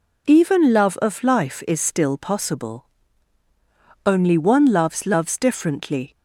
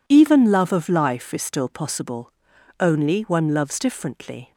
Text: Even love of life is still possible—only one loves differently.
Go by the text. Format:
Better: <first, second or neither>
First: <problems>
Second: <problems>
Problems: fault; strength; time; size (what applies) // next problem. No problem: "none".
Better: second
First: says "loves" twice; at 5.0 s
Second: none